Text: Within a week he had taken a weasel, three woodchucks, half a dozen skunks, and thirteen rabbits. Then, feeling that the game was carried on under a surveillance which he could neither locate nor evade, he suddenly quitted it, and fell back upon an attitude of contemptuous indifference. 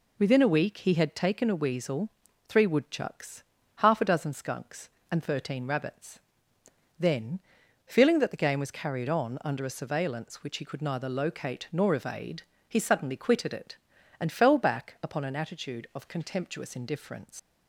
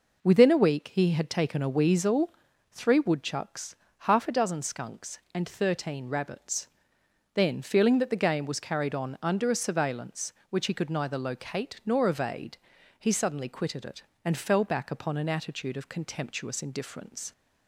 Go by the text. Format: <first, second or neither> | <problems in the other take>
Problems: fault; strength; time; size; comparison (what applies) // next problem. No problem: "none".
second | leaves "indifference" unfinished; at 17.3 s; 120 ms